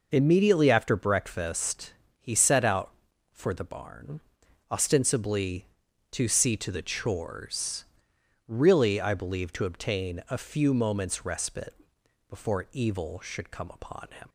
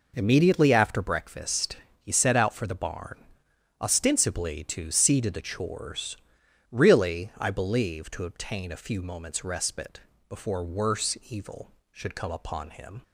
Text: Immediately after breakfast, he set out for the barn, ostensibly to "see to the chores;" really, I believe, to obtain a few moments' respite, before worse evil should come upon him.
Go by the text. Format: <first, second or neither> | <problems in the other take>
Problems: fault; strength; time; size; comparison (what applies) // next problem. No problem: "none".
second | skips "worse"; at 12.6 s